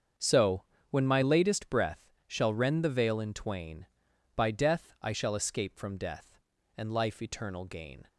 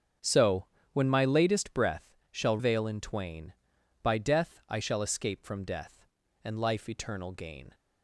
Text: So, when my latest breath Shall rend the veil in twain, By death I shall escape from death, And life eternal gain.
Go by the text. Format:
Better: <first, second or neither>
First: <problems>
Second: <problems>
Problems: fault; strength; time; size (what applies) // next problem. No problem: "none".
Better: first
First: starts louder than the rest; until 1.4 s; 7 dB // pauses between "breath" and "Shall"; slight; at 1.9 s; 0.28 s long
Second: starts louder than the rest; strong; until 1.5 s; 7.5 dB // pauses between "breath" and "Shall"; slight; at 2.0 s; 0.28 s long // skips "rend the"; at 2.5 s